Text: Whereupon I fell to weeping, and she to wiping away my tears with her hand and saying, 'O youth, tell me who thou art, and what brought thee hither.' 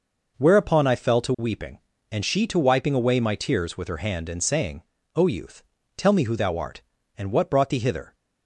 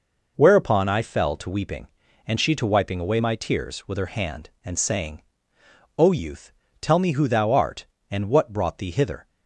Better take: neither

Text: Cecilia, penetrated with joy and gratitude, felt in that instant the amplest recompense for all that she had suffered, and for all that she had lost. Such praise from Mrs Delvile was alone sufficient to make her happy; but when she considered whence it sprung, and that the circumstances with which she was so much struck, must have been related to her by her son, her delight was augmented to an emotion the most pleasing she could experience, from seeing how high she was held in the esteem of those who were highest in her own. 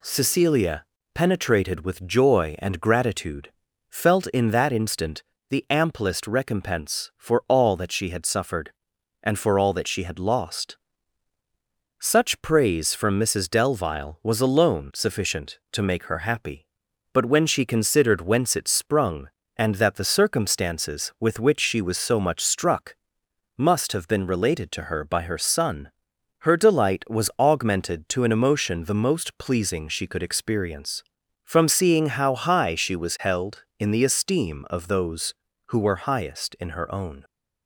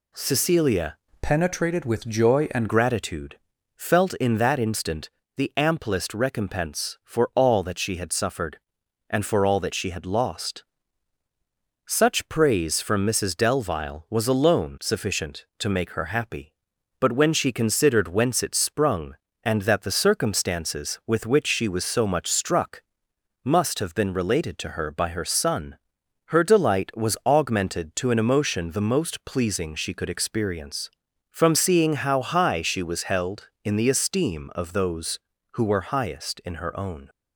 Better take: first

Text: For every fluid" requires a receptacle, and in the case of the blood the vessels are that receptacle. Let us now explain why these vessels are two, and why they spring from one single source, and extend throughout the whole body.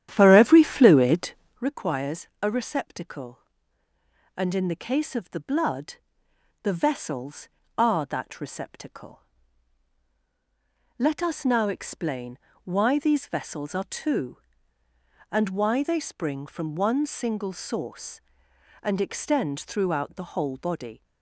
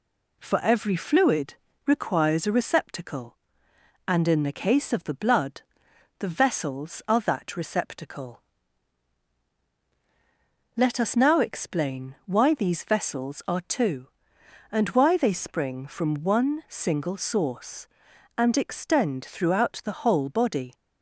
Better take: second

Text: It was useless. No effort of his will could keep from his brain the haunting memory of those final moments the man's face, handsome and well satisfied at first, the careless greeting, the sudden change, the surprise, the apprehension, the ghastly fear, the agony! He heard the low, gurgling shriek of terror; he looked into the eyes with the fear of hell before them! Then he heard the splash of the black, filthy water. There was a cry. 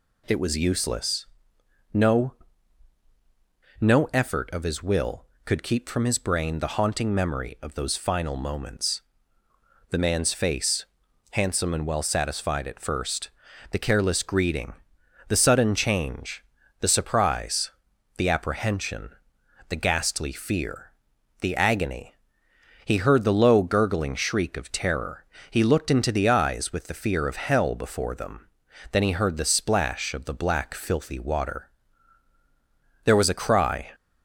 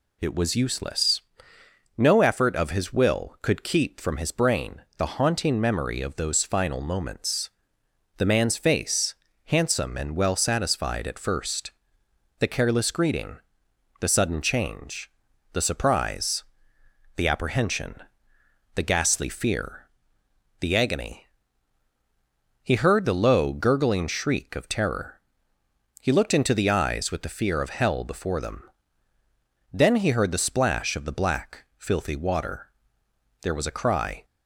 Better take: second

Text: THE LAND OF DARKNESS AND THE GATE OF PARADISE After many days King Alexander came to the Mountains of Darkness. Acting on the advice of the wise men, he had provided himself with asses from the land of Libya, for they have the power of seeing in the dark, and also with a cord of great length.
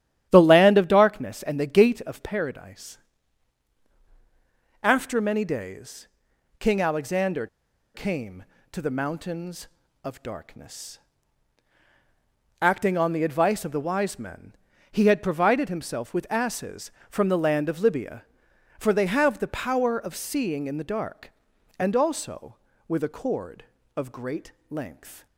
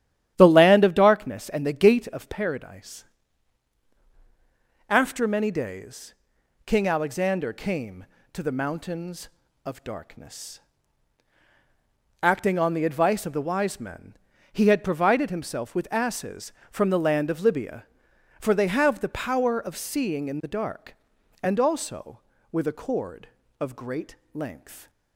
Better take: second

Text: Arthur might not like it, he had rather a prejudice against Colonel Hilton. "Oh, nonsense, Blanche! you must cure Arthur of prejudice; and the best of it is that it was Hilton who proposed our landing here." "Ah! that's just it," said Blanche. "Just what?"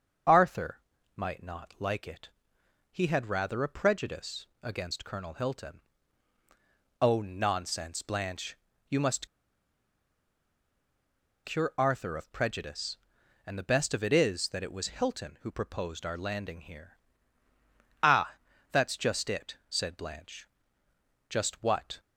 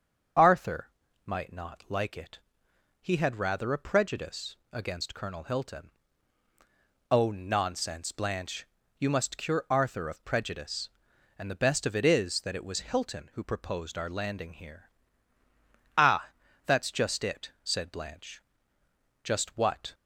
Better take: second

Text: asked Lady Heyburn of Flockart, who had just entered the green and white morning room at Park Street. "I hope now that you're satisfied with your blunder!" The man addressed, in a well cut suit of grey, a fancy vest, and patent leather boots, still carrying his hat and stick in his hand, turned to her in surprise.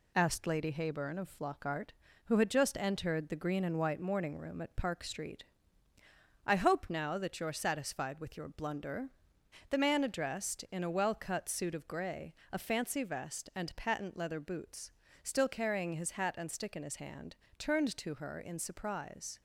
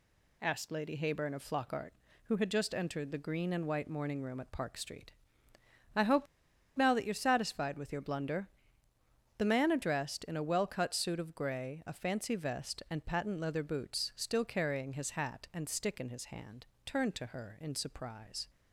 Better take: first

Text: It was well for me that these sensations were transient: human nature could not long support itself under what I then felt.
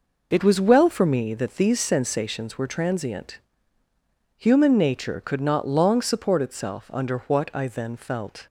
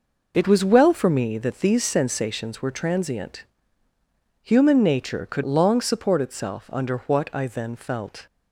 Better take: first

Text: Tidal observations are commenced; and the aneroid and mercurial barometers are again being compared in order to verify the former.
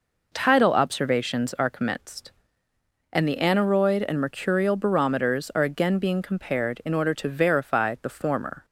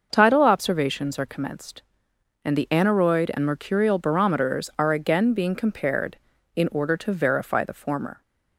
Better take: neither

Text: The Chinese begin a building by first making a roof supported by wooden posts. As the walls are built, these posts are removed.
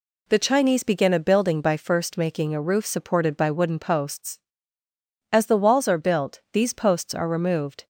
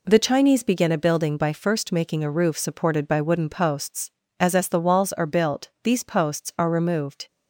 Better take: first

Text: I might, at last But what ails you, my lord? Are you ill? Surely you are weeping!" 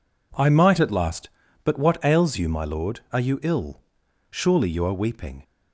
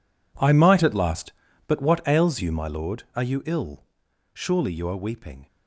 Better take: first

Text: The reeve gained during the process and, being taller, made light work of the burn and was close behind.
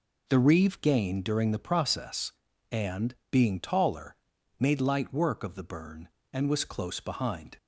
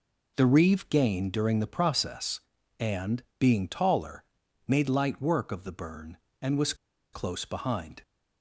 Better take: first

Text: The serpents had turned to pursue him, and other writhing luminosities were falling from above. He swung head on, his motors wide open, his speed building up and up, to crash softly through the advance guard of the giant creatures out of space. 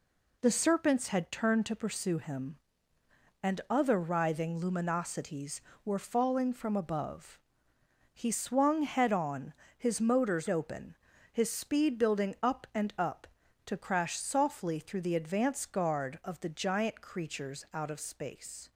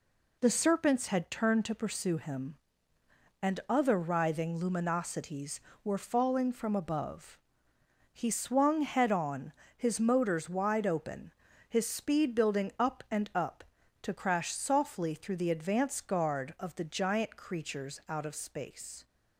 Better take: second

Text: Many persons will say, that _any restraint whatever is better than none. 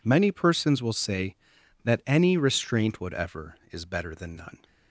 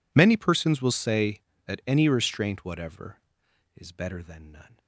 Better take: neither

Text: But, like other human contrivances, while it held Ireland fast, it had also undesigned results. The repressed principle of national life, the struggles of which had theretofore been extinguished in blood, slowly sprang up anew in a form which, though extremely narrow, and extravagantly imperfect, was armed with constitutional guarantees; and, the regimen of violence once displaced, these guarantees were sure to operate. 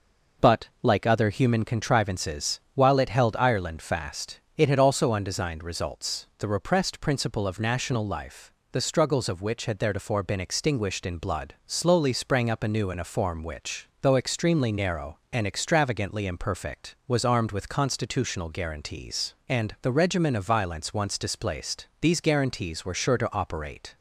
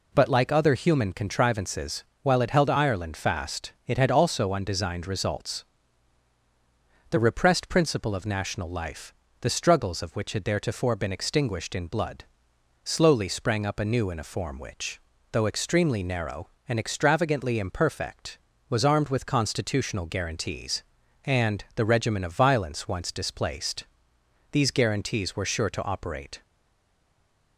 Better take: first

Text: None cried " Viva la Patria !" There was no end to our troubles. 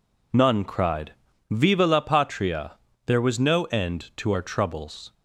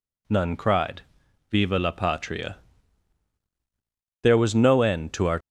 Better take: first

